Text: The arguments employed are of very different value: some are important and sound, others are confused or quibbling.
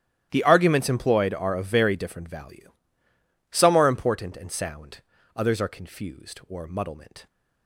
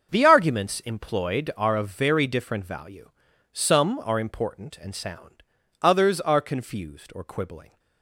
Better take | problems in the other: second | starts louder than the rest; strong; until 1.3 s; 12.5 dB; also in the second // says "muddlement" for "quibbling"; at 6.6 s

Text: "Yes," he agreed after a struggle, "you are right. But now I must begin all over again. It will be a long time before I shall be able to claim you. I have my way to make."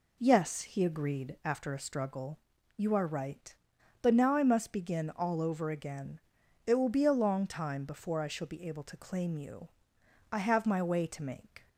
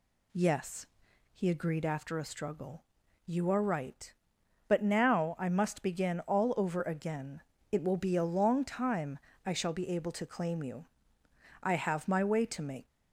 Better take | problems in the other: first | skips "before"; at 9.3 s

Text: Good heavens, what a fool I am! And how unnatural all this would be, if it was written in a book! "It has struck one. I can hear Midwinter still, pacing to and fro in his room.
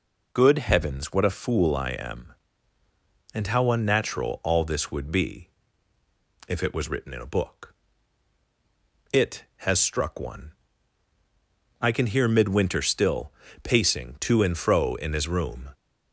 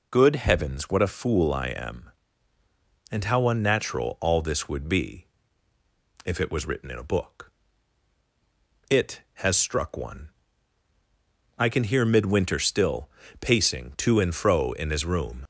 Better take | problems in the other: first | leaves "room" unfinished; at 15.4 s; 50 ms

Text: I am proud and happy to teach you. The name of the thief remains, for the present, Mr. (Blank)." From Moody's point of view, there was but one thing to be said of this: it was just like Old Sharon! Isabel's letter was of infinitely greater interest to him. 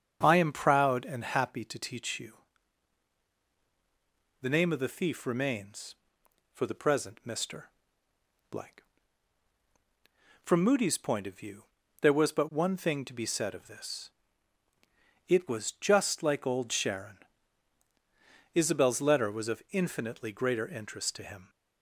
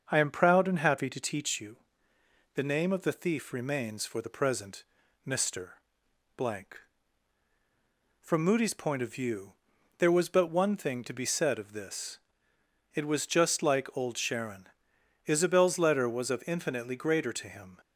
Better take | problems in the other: first | starts louder than the rest; until 1.1 s; 6.5 dB; strong in the first // skips "interest"; at 17.3 s

